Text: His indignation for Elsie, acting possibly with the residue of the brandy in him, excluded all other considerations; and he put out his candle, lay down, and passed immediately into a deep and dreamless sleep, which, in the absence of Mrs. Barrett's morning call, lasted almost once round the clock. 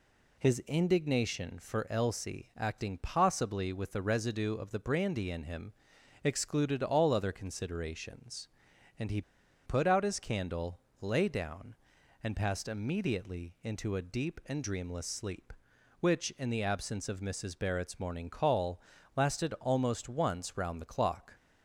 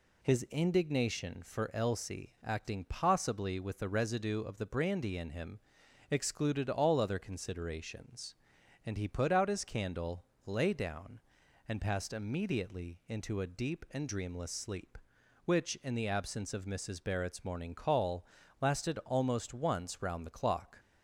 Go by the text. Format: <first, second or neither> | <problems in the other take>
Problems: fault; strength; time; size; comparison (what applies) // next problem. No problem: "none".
second | pauses between "he" and "put"; at 9.2 s; 0.44 s long